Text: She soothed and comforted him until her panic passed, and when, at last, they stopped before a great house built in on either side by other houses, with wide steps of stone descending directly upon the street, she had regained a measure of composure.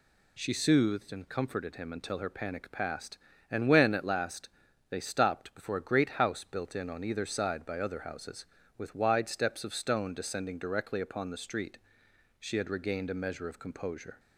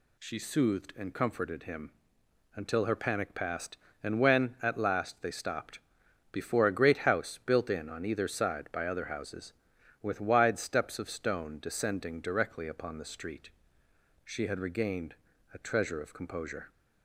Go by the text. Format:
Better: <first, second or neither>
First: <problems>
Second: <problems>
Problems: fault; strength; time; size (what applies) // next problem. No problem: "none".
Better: first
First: none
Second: pauses between "him" and "until"; noticeable; at 1.9 s; 0.64 s long // pauses between "stopped" and "before"; noticeable; at 5.7 s; 0.54 s long // pauses between "regained" and "a"; at 15.1 s; 0.40 s long // says "treasure" for "measure"; at 15.5 s